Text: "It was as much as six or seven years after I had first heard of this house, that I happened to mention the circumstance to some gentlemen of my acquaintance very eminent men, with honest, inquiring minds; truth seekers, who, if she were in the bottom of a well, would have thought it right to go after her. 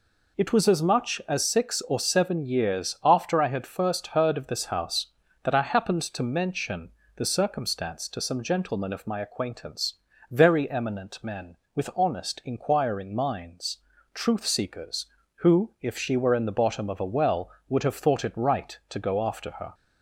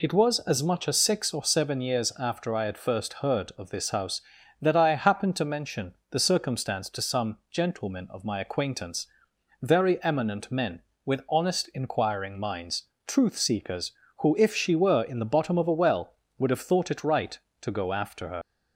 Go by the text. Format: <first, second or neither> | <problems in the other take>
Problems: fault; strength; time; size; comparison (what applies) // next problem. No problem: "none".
first | pauses between "mention" and "the"; slight; at 5.9 s; 0.16 s long; slight in the first // pauses between "acquaintance" and "very"; noticeable; at 9.0 s; 0.56 s long; also in the first // leaves "her" unfinished; at 18.4 s; 55 ms